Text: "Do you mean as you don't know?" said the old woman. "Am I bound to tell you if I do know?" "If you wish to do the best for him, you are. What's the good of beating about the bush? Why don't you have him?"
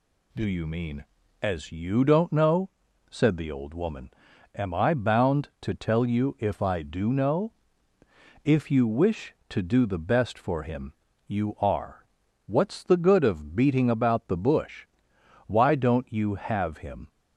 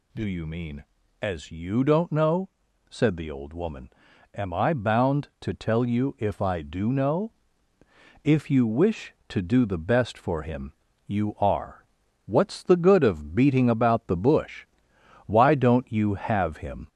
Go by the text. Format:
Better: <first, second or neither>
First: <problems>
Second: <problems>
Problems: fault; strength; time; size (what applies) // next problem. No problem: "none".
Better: first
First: none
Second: gets louder; slight; throughout; 2.5 dB